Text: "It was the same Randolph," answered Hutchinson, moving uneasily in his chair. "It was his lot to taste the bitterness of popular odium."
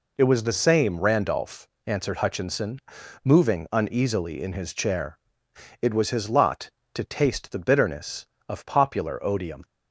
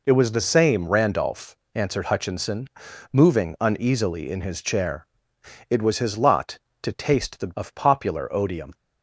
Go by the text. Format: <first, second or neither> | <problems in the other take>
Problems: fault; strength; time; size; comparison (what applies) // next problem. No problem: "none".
first | skips "bitterness"; at 7.5 s